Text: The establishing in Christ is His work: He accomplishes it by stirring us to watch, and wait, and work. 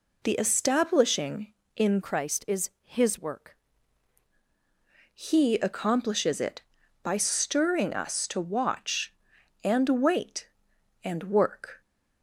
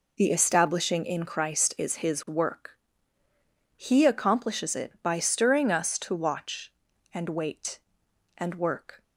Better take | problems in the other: second | changes voice from "Christ" to "work"; from 2.0 to 3.5 s; 1.5 s long

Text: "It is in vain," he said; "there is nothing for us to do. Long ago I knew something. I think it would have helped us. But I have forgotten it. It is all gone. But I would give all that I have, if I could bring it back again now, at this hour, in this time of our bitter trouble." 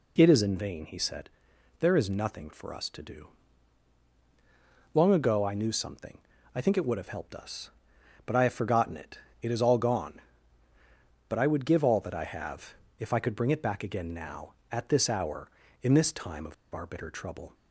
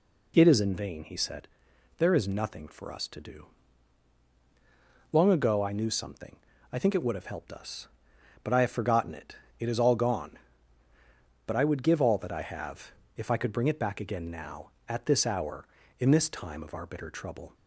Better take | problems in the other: second | pauses between "of" and "our"; slight; at 16.5 s; 0.19 s long

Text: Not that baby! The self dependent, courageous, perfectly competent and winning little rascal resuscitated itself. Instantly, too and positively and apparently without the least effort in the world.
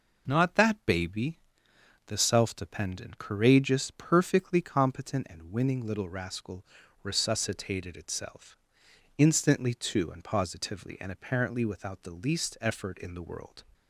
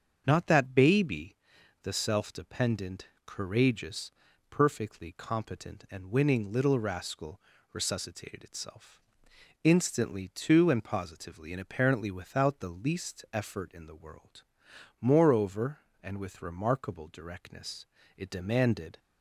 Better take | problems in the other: first | starts louder than the rest; strong; until 1.2 s; 7 dB // pauses between "rascal" and "resuscitated"; slight; at 7.4 s; 0.32 s long; also in the first // goes on to say "Moreover and with remarkable directness it demanded"; strong; from 15.0 s on; 3.9 s long

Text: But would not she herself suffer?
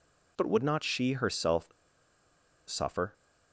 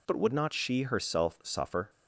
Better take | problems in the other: second | pauses between "herself" and "suffer"; noticeable; at 1.6 s; 0.97 s long

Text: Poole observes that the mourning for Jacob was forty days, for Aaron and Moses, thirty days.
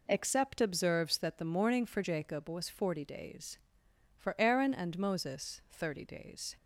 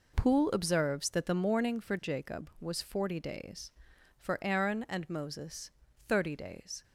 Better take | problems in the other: second | says "Except" for "Poole"; at 0.0 s

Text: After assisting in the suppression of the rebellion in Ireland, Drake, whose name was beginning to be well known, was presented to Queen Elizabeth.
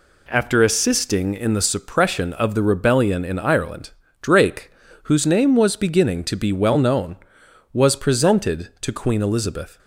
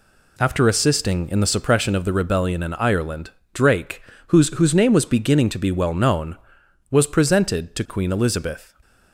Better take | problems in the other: first | says "whose" twice; at 4.4 s

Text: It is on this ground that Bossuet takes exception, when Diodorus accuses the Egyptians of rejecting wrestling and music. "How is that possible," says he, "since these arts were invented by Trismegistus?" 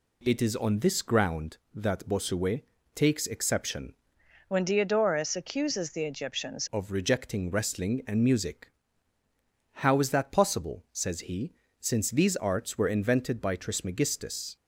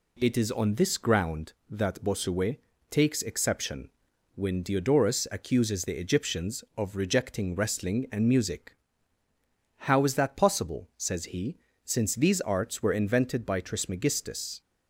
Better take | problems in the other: second | pauses between "Bossuet" and "takes"; slight; at 2.6 s; 0.32 s long; slight in the second // changes voice from "when" to "Egyptians"; from 4.4 to 6.6 s; 2.2 s long

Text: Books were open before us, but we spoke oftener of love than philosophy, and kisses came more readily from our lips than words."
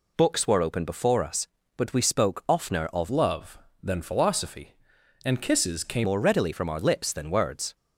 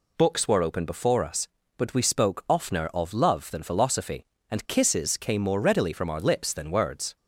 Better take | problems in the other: second | changes voice from "love" to "came"; from 3.0 to 6.0 s; 3.0 s long

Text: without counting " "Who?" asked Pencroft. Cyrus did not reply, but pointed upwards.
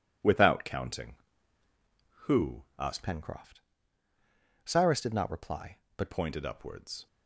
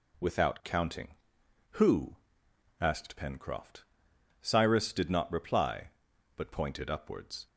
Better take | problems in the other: second | changes voice from "Pencroft" to "but"; from 3.0 to 6.1 s; 3.1 s long

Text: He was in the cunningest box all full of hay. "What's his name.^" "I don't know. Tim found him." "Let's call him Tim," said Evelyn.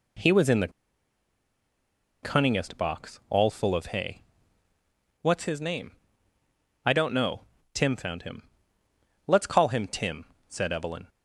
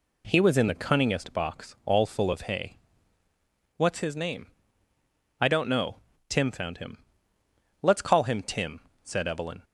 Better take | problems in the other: second | pauses between "the" and "cunningest"; strong; at 0.7 s; 1.5 s long

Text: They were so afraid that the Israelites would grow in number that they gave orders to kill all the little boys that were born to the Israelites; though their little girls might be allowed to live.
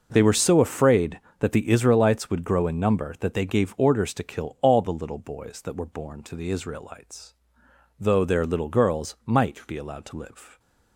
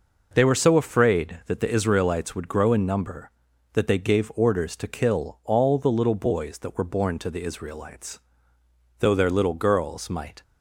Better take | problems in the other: first | stops before "be allowed to live"; at 10.4 s

